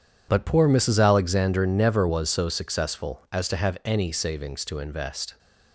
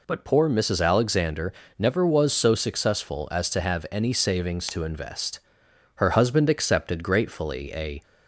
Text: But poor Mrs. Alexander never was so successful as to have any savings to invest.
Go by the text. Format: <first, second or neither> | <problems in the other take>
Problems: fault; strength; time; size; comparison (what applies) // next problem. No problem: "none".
first | pauses between "Alexander" and "never"; slight; at 1.5 s; 0.26 s long // goes on to say "Her husband accepted gratefully a"; strong; from 5.9 s on; 2.0 s long